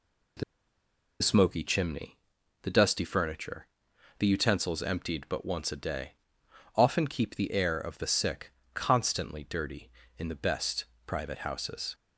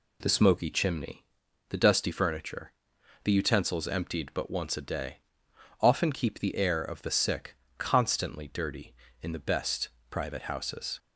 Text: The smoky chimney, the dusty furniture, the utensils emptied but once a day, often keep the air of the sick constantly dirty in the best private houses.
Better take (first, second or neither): second